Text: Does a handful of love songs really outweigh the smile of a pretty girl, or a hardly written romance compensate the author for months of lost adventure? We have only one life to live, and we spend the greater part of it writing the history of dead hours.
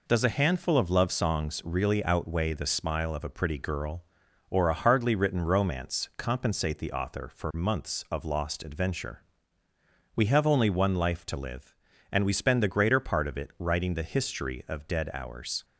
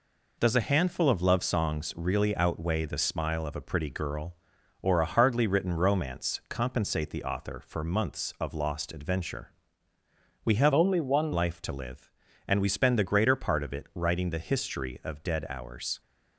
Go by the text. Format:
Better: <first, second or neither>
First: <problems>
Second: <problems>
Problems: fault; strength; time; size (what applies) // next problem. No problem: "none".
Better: first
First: none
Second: changes voice from "only" to "one"; from 10.7 to 11.3 s; 0.6 s long